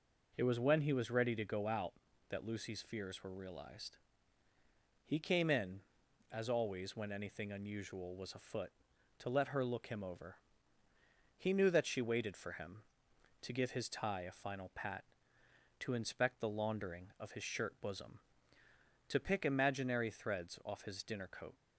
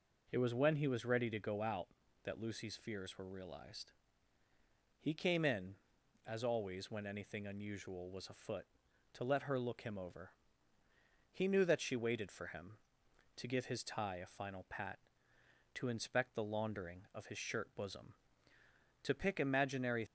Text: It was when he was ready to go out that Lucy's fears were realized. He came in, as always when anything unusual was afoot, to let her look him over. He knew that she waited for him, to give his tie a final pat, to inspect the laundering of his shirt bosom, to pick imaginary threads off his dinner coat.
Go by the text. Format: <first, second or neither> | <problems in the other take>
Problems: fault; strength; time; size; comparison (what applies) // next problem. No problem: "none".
first | stops before "threads off his dinner coat"; at 20.0 s